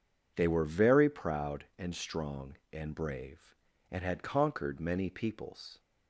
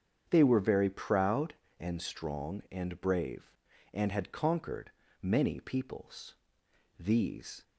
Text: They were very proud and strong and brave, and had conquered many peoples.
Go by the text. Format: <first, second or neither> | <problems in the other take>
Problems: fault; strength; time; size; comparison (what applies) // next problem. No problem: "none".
first | starts louder than the rest; strong; until 1.2 s; 7.5 dB // pauses between "conquered" and "many"; slight; at 4.9 s; 0.30 s long // goes on to say "These"; noticeable; from 6.9 s on; 0.64 s long